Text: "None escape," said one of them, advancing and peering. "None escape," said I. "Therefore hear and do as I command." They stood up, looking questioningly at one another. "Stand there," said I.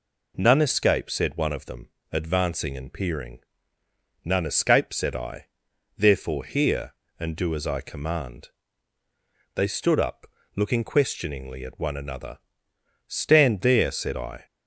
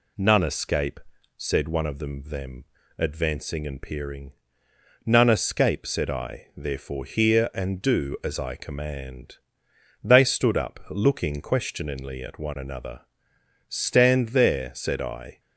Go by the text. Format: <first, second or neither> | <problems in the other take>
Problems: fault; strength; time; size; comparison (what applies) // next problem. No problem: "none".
first | says "them" twice; at 2.2 s